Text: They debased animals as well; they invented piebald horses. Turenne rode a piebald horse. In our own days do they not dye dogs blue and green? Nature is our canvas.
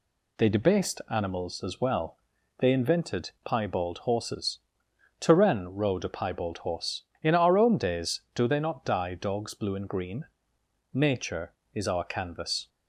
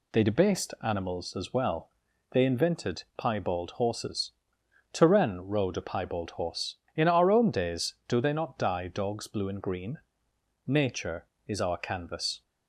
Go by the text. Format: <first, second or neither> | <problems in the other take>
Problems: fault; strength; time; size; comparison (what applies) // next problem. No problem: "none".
neither | none